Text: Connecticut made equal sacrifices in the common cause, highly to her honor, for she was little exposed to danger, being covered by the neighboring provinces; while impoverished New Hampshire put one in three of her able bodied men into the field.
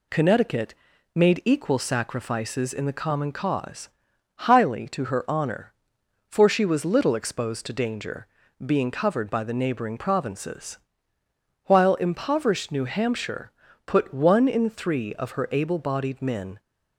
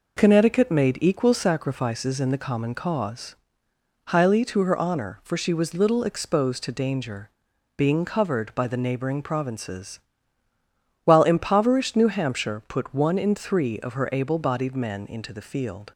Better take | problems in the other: second | pauses between "Connecticut" and "made"; at 0.7 s; 0.40 s long // pauses between "Hampshire" and "put"; at 13.4 s; 0.38 s long // stops before "into the field"; at 16.5 s

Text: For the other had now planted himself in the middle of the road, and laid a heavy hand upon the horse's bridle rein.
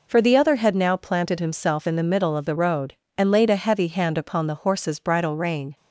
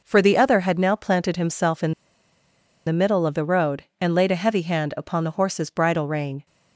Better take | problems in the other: first | pauses between "in" and "the"; noticeable; at 1.9 s; 0.94 s long

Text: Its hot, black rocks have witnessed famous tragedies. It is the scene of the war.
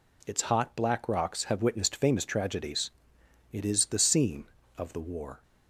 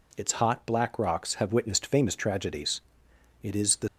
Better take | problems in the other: first | stops before "scene of the war"; at 3.8 s

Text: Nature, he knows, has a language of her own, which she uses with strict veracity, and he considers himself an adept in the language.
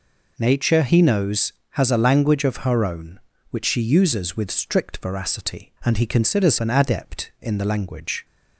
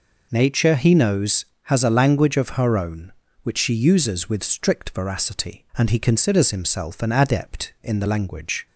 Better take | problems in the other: second | skips "himself"; at 6.5 s

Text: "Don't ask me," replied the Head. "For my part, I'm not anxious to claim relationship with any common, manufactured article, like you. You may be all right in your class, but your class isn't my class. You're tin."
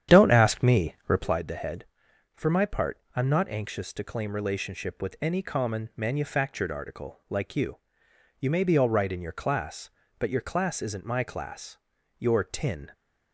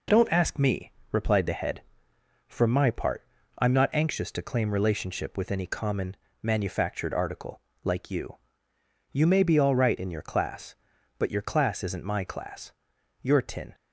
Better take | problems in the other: second | starts louder than the rest; strong; until 1.4 s; 9.5 dB

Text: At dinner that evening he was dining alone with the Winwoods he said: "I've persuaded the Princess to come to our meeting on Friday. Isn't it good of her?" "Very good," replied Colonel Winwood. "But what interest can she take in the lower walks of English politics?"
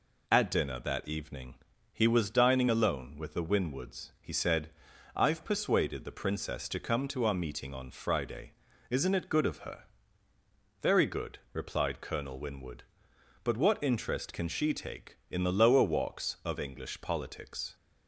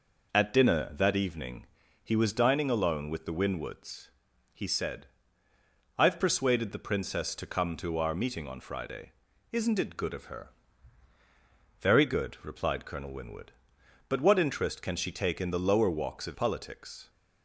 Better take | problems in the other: first | pauses between "evening" and "he"; at 1.6 s; 0.38 s long; also in the first // pauses between "Winwoods" and "he"; at 4.1 s; 0.42 s long // skips "English"; at 16.3 s

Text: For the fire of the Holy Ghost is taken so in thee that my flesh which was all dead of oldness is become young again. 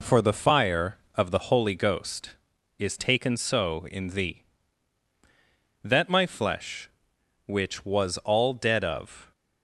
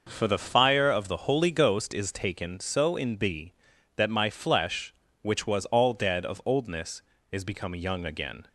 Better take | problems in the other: second | stops before "oldness is become young again"; at 9.3 s

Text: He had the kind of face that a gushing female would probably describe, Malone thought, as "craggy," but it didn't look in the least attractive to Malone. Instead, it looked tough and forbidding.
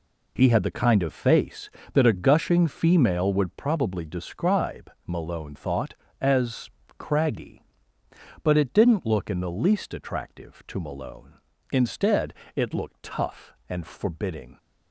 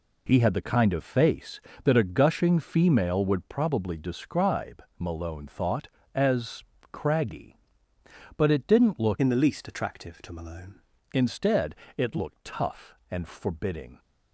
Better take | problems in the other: first | pauses between "as" and "craggy"; slight; at 6.6 s; 0.26 s long; slight in the first // changes voice from "in" to "Malone"; from 9.2 to 10.8 s; 1.6 s long

